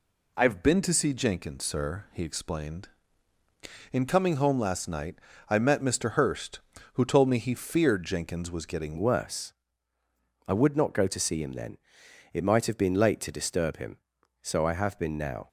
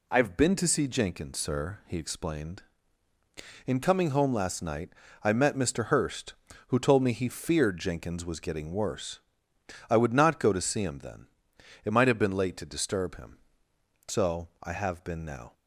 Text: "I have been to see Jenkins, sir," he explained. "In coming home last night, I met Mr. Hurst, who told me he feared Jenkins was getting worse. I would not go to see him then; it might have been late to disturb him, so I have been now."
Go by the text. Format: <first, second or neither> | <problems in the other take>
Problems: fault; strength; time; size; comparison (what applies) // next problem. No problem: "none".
second | changes voice at "worse"; from 8.9 s on; 6.5 s long